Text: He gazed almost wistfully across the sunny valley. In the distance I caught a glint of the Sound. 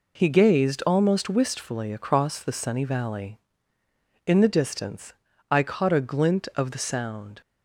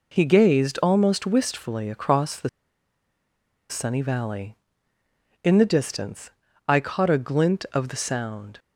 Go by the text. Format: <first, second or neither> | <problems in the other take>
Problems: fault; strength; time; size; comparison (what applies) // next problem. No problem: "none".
first | pauses between "the" and "sunny"; at 2.4 s; 1.2 s long // pauses between "distance" and "I"; at 6.2 s; 0.40 s long; also in the first